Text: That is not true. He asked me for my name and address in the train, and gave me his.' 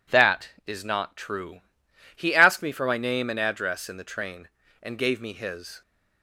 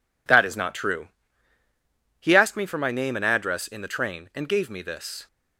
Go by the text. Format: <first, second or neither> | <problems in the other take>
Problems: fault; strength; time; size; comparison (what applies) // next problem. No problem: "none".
first | says "this" for "his"; at 4.8 s